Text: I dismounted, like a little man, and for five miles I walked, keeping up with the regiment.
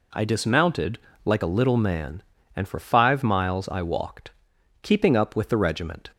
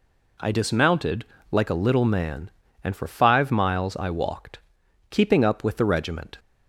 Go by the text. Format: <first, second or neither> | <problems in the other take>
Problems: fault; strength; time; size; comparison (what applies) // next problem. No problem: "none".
neither | none